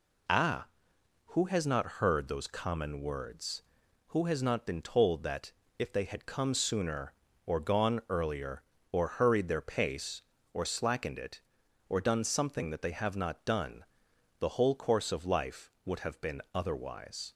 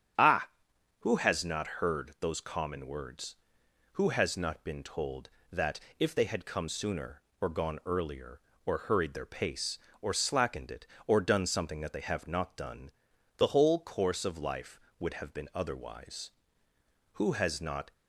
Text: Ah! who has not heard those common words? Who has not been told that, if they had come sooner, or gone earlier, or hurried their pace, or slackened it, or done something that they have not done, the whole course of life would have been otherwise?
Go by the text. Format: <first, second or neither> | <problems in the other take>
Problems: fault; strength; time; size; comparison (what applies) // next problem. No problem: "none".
first | starts louder than the rest; strong; until 1.7 s; 8 dB // goes on to say "Who has not"; noticeable; from 17.1 s on; 0.78 s long